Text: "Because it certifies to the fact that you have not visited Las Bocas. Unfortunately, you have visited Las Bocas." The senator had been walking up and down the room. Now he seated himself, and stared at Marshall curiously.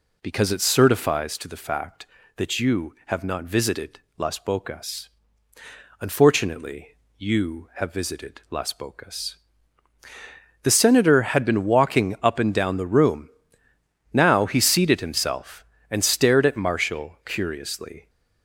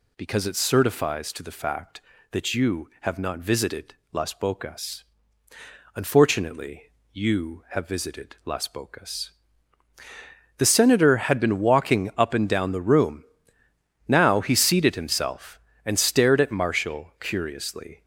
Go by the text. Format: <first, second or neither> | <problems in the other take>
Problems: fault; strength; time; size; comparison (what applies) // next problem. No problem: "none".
second | starts louder than the rest; slight; until 1.4 s; 2.5 dB // pauses between "visited" and "Las"; slight; at 3.9 s; 0.18 s long; slight in the second